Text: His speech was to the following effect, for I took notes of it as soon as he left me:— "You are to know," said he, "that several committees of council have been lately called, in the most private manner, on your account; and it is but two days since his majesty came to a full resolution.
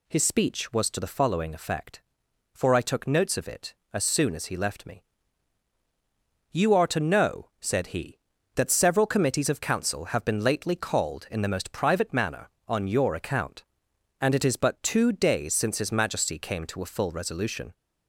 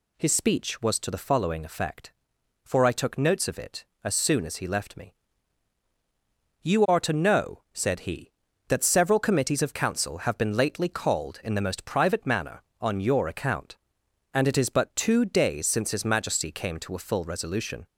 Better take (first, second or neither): neither